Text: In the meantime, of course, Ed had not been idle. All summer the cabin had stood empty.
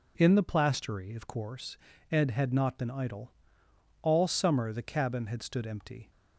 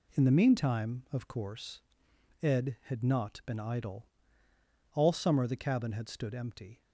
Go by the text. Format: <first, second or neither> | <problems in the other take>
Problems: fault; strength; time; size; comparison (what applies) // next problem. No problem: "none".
second | says "plastery" for "meantime"; at 0.4 s